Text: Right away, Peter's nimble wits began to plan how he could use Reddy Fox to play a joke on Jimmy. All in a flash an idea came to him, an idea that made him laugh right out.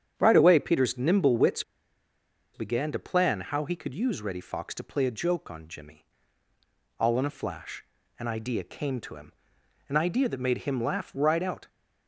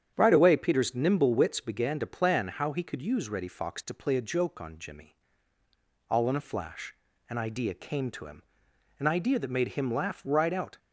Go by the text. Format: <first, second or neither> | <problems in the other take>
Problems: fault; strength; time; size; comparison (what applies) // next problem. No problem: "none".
second | starts louder than the rest; strong; until 1.1 s; 8.5 dB; strong in the second // pauses between "wits" and "began"; noticeable; at 1.6 s; 0.91 s long // pauses between "flash" and "an"; slight; at 7.8 s; 0.34 s long; slight in the second